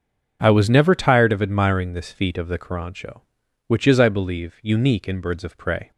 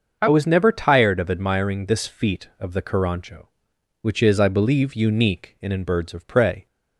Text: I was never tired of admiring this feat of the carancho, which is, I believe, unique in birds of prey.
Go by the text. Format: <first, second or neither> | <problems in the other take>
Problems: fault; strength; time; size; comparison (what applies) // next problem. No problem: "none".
first | starts louder than the rest; until 1.2 s; 6.5 dB // says "in" twice; at 5.7 s